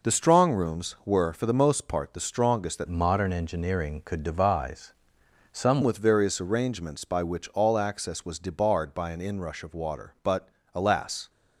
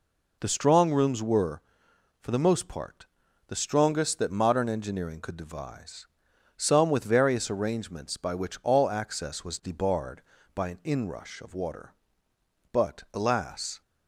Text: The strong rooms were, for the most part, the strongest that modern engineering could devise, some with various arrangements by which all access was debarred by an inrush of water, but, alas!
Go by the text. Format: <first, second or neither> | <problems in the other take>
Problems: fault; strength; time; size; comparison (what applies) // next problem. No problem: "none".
second | changes voice from "modern" to "some"; from 2.8 to 5.8 s; 3.0 s long